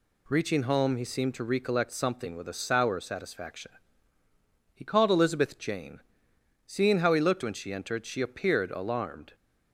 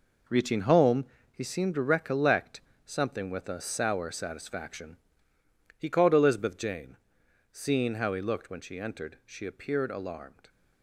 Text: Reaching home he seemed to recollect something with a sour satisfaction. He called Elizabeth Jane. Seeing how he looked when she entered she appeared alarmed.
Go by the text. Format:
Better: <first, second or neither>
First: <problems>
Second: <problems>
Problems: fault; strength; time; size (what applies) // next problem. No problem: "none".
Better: first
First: none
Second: gets quieter; strong; throughout; 9.5 dB // pauses between "home" and "he"; slight; at 1.0 s; 0.28 s long // pauses between "recollect" and "something"; slight; at 2.6 s; 0.24 s long